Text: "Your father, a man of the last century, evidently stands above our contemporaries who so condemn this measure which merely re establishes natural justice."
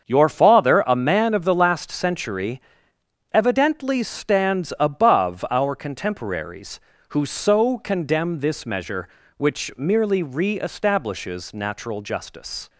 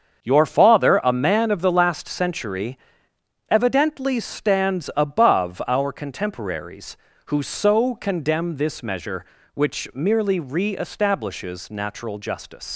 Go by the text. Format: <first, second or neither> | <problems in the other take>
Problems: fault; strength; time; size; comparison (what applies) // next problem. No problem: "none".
first | starts louder than the rest; until 1.2 s; 7 dB; also in the first // leaves "justice" unfinished; at 12.7 s; 110 ms